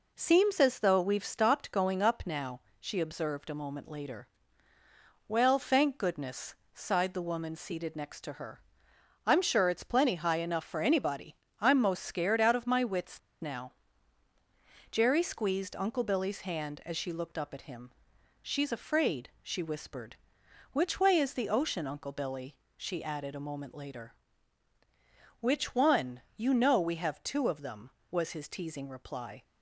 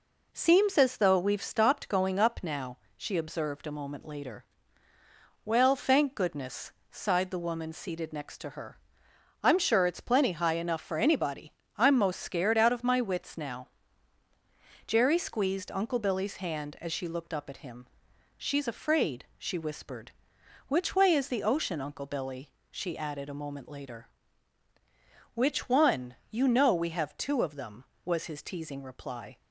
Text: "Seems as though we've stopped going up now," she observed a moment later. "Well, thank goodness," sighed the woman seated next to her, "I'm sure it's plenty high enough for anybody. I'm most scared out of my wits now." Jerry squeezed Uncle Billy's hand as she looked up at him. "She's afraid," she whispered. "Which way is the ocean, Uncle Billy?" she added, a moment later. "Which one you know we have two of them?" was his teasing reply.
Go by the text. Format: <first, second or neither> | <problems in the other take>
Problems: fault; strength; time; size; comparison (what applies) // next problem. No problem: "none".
second | pauses between "wits" and "now"; slight; at 13.1 s; 0.21 s long // pauses between "one" and "you"; slight; at 26.1 s; 0.16 s long; slight in the second